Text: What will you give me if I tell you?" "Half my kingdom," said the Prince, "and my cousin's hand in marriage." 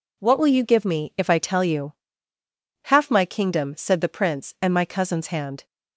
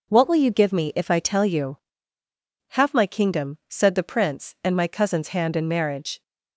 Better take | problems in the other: second | stops before "in marriage"; at 5.6 s

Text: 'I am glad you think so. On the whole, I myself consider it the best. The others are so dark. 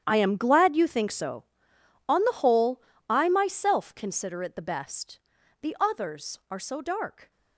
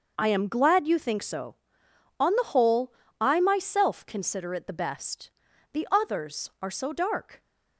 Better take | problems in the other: second | gets quieter; strong; throughout; 16 dB // starts louder than the rest; strong; until 1.0 s; 9.5 dB; noticeable in the second

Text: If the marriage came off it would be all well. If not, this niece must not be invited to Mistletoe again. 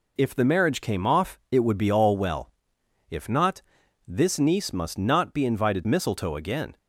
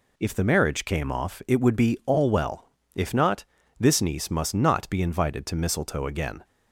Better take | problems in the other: second | skips "to"; at 5.8 s

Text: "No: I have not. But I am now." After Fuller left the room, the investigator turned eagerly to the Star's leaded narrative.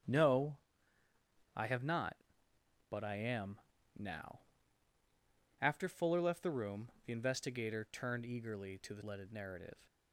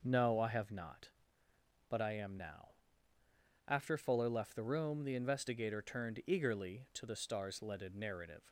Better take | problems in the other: second | starts louder than the rest; strong; until 2.0 s; 9.5 dB // pauses between "am" and "now"; slight; at 3.6 s; 0.36 s long // skips "Star's"; at 9.0 s

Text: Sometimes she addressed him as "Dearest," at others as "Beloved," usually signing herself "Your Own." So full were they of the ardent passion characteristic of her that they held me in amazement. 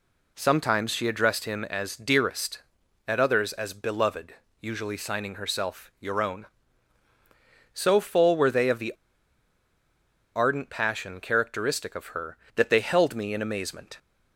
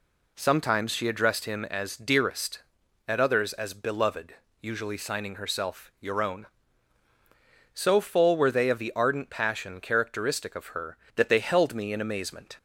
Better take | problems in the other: second | pauses between "the" and "ardent"; strong; at 8.9 s; 1.4 s long

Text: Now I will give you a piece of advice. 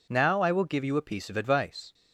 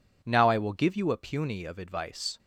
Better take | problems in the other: first | says "puny" for "piece"; at 1.1 s

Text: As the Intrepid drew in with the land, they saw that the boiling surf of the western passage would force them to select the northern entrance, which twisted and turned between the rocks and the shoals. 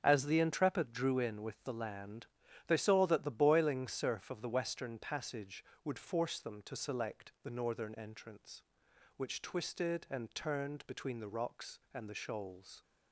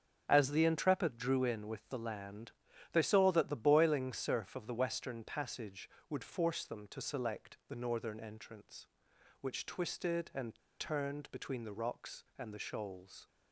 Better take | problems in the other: first | starts louder than the rest; strong; until 1.2 s; 7.5 dB; strong in the first // pauses between "and" and "turned"; slight; at 10.5 s; 0.21 s long

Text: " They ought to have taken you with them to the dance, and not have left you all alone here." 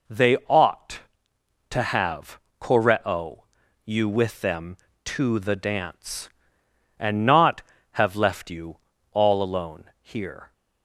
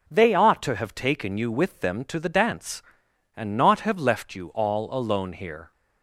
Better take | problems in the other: second | says "koreo" for "taken"; at 2.6 s // pauses between "you" and "all"; slight; at 8.7 s; 0.32 s long

